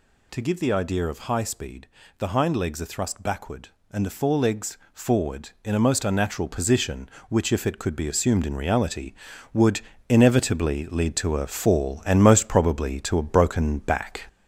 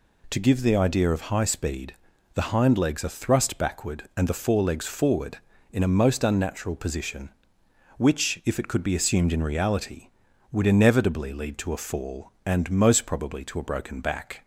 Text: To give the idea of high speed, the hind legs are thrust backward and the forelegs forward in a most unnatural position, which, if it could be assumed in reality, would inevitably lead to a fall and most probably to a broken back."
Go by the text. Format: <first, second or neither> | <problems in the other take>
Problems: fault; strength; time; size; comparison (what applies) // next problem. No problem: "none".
second | gets louder; noticeable; throughout; 5 dB // pauses between "forelegs" and "forward"; slight; at 4.7 s; 0.16 s long // pauses between "would" and "inevitably"; slight; at 9.7 s; 0.30 s long